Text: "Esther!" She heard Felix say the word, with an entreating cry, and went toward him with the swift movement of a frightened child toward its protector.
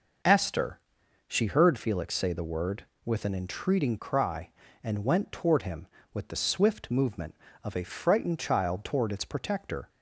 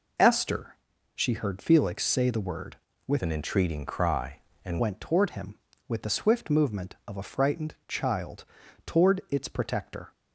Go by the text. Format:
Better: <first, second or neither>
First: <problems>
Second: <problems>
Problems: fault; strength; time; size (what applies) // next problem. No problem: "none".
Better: first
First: none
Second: changes voice from "an" to "and"; from 3.2 to 4.8 s; 1.6 s long // pauses between "child" and "toward"; at 8.4 s; 0.42 s long